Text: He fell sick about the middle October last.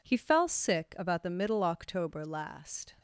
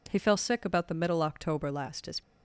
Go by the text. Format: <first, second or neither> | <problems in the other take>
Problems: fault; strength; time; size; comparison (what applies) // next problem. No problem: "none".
first | goes on to say "His"; slight; from 2.0 s on; 0.16 s long